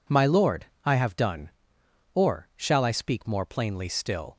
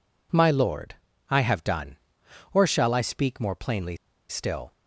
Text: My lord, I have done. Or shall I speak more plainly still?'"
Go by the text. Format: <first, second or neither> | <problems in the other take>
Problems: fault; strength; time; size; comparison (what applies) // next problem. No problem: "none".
first | pauses between "plainly" and "still"; slight; at 3.9 s; 0.32 s long